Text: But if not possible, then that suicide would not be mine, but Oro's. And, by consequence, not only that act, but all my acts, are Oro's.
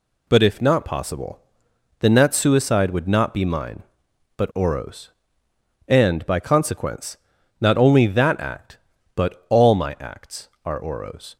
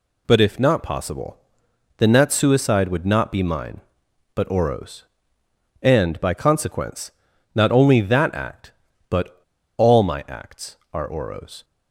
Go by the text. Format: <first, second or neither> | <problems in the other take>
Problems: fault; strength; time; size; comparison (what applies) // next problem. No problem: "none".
first | pauses between "but" and "all"; at 9.3 s; 0.40 s long